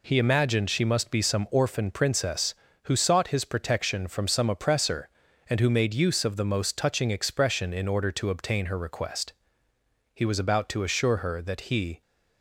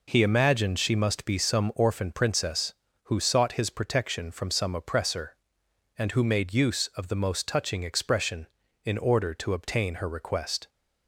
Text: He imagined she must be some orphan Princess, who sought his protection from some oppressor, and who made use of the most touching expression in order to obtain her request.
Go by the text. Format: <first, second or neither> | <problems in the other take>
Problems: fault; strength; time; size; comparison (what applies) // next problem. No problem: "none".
second | goes on to say "He was about to assure her that he"; strong; from 10.1 s on; 1.8 s long